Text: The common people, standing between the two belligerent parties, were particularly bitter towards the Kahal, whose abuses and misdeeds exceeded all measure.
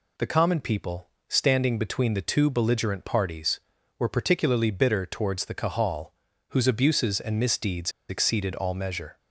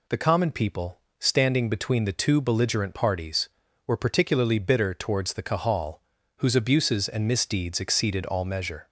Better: second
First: pauses between "misdeeds" and "exceeded"; slight; at 7.9 s; 0.18 s long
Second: none

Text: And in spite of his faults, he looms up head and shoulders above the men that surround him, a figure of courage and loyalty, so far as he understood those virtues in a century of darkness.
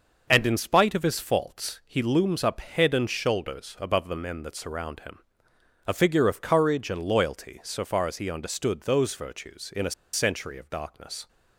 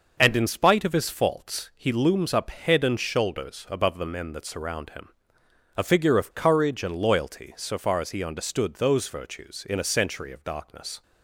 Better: second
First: pauses between "a" and "century"; slight; at 9.9 s; 0.21 s long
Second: none

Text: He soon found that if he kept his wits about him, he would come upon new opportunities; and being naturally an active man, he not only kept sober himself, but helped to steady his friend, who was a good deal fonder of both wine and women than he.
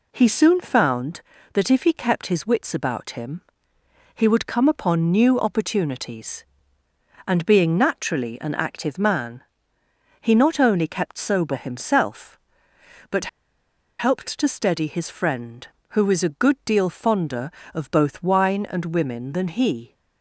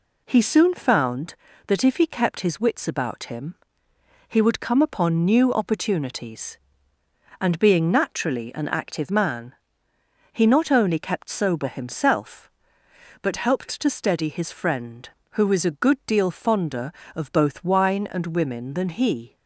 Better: second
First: pauses between "but" and "helped"; noticeable; at 13.2 s; 0.71 s long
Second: none

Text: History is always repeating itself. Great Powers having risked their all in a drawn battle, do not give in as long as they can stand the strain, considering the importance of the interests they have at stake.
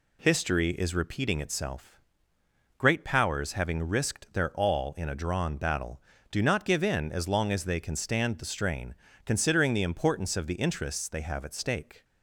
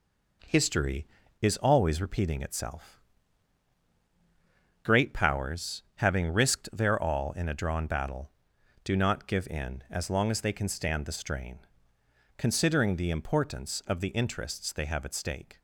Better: second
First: skips "always"; at 0.9 s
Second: none

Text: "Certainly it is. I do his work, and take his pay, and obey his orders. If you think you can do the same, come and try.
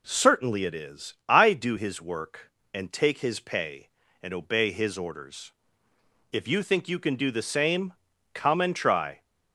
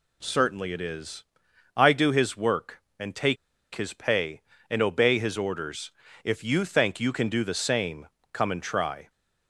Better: first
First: none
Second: pauses between "take" and "his"; at 3.3 s; 0.38 s long

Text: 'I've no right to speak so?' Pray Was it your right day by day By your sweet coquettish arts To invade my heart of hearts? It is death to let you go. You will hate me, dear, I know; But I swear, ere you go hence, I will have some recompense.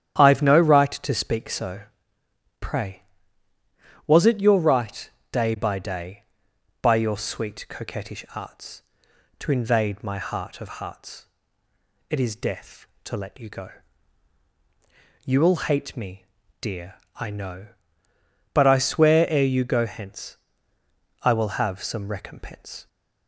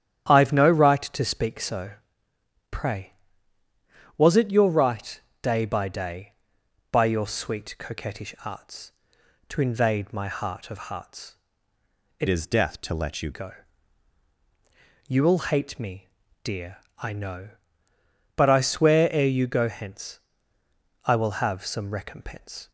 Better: first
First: starts louder than the rest; strong; until 1.1 s; 10 dB // pauses between "right" and "day"; slight; at 5.1 s; 0.20 s long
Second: starts louder than the rest; strong; until 1.3 s; 10 dB // pauses between "right" and "day"; slight; at 5.2 s; 0.20 s long // changes voice from "is" to "you"; from 12.2 to 13.3 s; 1.1 s long

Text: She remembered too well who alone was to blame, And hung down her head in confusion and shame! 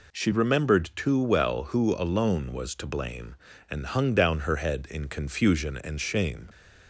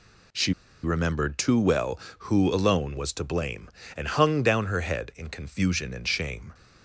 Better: first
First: none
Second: pauses between "She" and "remembered"; slight; at 0.5 s; 0.30 s long

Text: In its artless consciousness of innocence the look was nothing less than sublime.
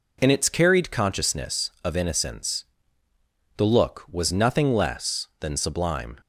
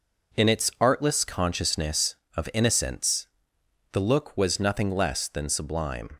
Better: second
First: says "carried" for "artless"; at 0.4 s // pauses between "innocence" and "the"; noticeable; at 2.6 s; 0.90 s long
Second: pauses between "innocence" and "the"; noticeable; at 3.2 s; 0.64 s long

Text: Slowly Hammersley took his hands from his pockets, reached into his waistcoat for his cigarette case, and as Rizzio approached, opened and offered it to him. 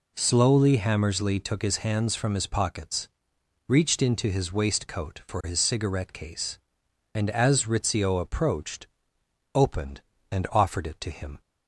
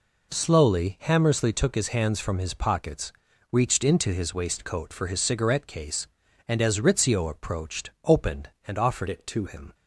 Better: first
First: none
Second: changes voice from "it" to "to"; from 9.0 to 9.4 s; 0.4 s long

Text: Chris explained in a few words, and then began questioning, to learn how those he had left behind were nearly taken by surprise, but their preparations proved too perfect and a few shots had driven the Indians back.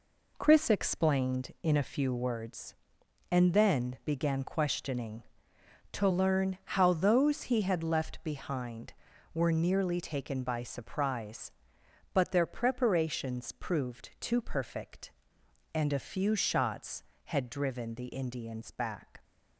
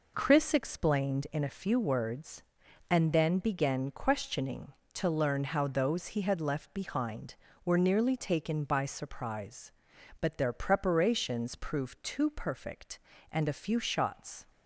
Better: first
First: none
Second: stops before "had driven the Indians back"; at 14.4 s

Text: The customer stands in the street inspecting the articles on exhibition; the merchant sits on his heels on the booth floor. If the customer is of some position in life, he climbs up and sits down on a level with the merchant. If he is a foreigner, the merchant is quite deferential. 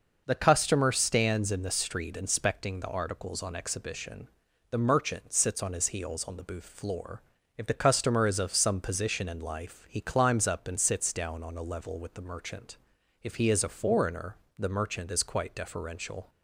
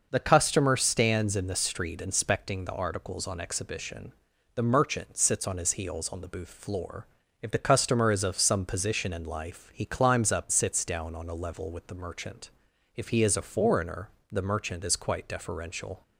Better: first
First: none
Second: skips "and"; at 10.5 s

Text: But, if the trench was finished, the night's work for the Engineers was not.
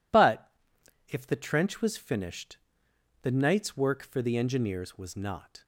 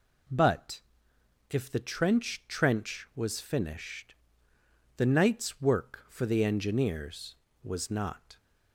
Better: first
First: none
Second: says "trench" twice; at 2.4 s

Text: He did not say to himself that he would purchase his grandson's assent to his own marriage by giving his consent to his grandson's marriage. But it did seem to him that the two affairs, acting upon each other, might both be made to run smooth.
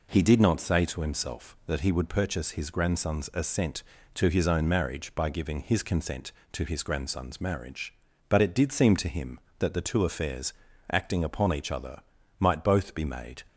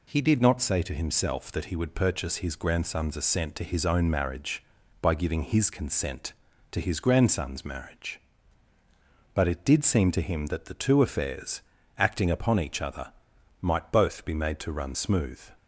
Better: second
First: stops before "to run smooth"; at 13.4 s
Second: none

